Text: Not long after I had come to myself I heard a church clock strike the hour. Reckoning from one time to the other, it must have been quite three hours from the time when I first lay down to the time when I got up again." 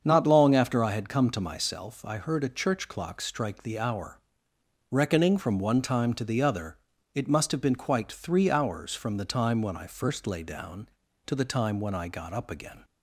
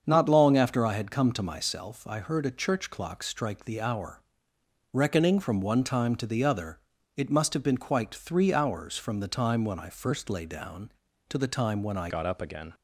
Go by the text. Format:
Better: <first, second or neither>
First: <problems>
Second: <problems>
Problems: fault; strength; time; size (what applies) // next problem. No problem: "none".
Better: first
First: starts louder than the rest; strong; until 1.0 s; 7 dB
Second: starts louder than the rest; strong; until 1.0 s; 7 dB // changes voice at "got"; from 12.0 s on; 0.7 s long